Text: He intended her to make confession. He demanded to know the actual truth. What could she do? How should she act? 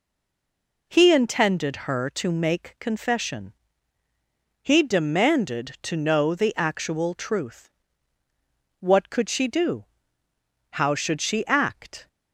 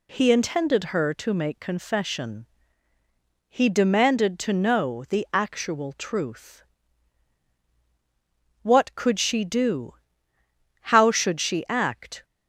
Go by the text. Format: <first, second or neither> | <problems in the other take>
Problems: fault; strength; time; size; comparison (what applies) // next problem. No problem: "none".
second | stays silent before the first word; slight; until 0.8 s; 0.8 s long